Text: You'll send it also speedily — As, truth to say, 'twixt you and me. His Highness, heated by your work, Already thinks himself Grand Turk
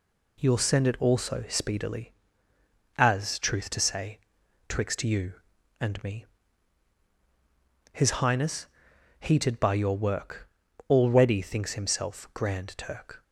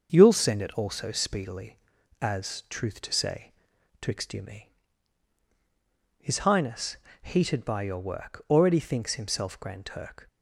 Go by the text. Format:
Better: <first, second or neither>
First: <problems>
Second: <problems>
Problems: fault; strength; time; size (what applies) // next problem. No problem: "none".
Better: first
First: none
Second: starts louder than the rest; until 1.1 s; 6.5 dB // skips "and"; at 4.4 s